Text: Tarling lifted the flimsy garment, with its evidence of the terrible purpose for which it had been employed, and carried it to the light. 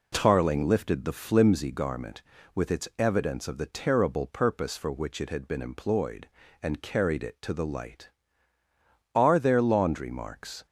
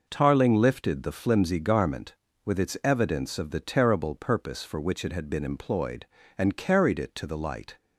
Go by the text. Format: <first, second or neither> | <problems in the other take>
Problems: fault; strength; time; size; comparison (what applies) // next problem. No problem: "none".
second | goes on to say "Are there laundry marks"; from 9.1 s on; 1.5 s long